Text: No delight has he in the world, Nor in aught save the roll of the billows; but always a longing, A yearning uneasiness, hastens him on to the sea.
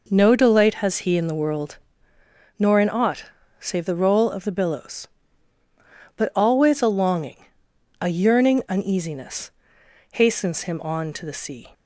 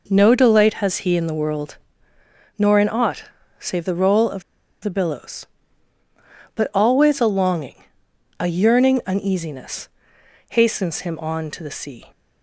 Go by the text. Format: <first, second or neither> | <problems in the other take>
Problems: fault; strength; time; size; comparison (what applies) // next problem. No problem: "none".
first | pauses between "aught" and "save"; slight; at 3.2 s; 0.34 s long; slight in the first // pauses between "of" and "the"; at 4.4 s; 0.41 s long